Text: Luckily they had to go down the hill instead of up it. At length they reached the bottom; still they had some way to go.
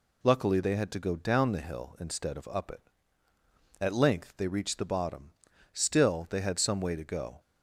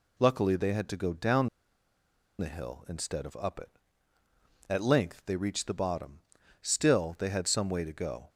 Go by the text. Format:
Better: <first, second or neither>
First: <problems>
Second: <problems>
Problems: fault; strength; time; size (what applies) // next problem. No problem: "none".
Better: first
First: none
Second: pauses between "down" and "the"; noticeable; at 1.4 s; 0.92 s long